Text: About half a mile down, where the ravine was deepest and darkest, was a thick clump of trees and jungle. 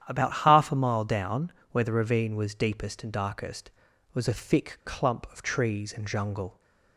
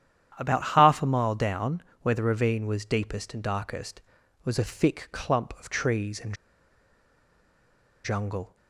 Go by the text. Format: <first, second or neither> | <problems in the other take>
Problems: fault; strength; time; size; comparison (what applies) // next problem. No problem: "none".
first | starts louder than the rest; strong; until 1.3 s; 10 dB; strong in the first // pauses between "and" and "jungle"; strong; at 6.3 s; 1.7 s long